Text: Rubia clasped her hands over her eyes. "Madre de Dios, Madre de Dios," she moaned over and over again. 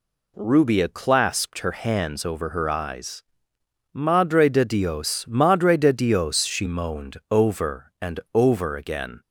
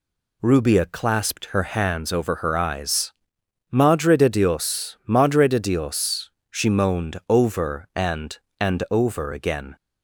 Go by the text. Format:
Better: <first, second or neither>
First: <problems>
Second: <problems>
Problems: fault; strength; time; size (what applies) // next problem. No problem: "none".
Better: first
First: none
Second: says "and" twice; at 8.5 s